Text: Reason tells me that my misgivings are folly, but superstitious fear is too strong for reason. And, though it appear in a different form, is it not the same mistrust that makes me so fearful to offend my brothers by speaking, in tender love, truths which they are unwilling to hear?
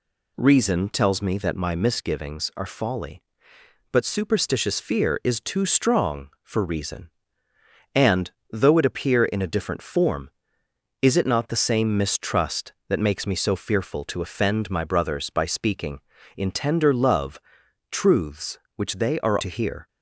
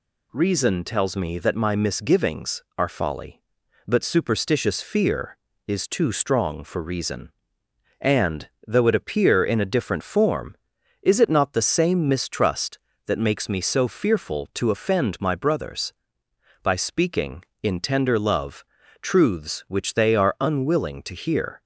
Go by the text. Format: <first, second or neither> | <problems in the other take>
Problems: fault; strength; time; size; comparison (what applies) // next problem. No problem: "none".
second | skips "unwilling"; at 19.4 s